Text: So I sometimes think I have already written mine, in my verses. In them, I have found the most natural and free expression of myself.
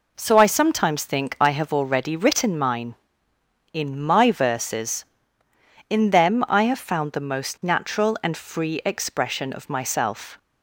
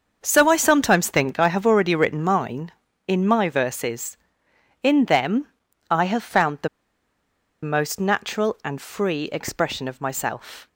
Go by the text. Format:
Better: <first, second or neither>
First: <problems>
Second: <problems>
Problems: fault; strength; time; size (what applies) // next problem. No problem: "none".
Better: first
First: none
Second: starts louder than the rest; until 1.2 s; 6.5 dB // pauses between "the" and "most"; noticeable; at 6.6 s; 0.95 s long